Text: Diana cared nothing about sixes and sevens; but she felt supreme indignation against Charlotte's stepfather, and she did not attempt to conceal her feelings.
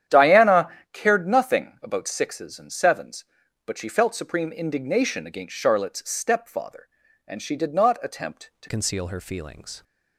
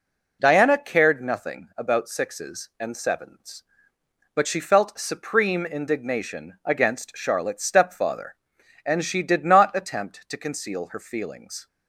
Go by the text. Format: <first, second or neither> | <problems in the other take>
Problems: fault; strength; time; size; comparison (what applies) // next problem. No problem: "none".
second | starts louder than the rest; strong; until 1.3 s; 10 dB // pauses between "Diana" and "cared"; slight; at 0.6 s; 0.24 s long // changes voice at "conceal"; from 8.6 s on; 1.2 s long